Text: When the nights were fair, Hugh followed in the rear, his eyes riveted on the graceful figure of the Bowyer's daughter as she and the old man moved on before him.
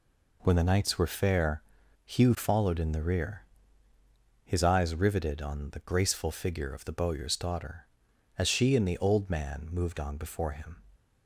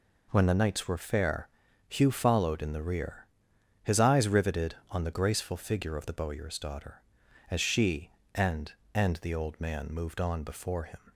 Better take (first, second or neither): first